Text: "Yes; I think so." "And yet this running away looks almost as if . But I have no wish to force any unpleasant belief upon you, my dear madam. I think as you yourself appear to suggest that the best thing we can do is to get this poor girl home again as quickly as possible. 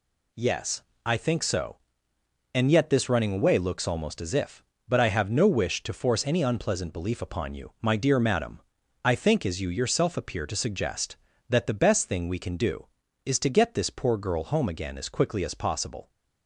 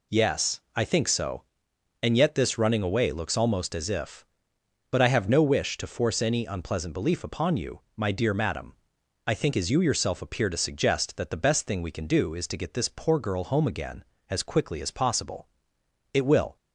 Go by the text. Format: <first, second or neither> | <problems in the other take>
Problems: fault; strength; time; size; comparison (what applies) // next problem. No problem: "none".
first | goes on to say "It will"; slight; from 16.1 s on; 0.42 s long